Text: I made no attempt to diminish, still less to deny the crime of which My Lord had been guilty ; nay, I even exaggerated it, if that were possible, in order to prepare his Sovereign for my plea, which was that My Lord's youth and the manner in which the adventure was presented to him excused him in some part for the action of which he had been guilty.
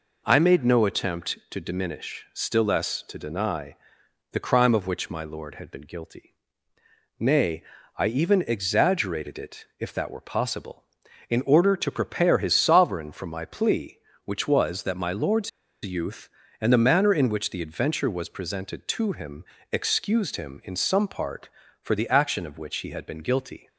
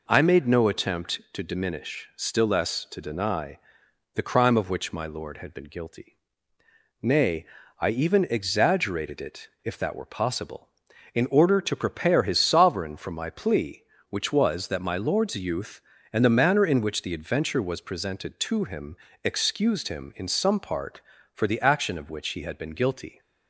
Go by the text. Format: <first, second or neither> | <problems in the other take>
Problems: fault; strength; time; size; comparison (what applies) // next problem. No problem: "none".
second | pauses between "deny" and "the"; noticeable; at 3.7 s; 0.56 s long; noticeable in the second // pauses between "Lord's" and "youth"; slight; at 15.4 s; 0.34 s long // pauses between "him" and "excused"; slight; at 19.4 s; 0.28 s long; slight in the second